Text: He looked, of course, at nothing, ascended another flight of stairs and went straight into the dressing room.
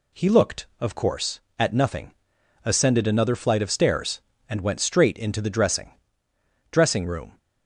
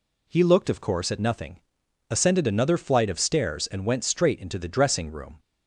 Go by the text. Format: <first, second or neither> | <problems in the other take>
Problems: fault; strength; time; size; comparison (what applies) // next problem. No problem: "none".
second | says "dressing" twice; at 6.7 s